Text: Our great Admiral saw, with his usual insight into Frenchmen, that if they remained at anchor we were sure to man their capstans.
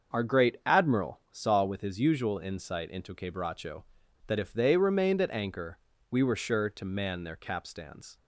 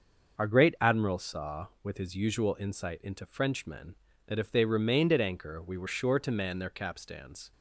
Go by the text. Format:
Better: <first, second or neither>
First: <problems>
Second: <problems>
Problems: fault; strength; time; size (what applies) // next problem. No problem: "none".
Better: second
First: starts louder than the rest; until 1.3 s; 6.5 dB // says "Quebracho" for "Frenchmen"; at 3.1 s // pauses between "anchor" and "we"; slight; at 5.7 s; 0.32 s long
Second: starts louder than the rest; noticeable; until 1.4 s; 6 dB